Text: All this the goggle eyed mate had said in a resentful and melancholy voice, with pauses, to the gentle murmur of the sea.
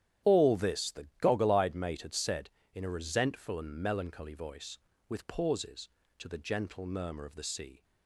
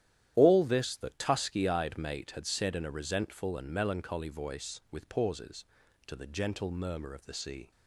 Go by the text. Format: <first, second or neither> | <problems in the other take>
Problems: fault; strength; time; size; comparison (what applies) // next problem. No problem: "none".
first | starts louder than the rest; strong; until 1.3 s; 11.5 dB; strong in the first // says "tusky" for "goggle"; at 1.0 s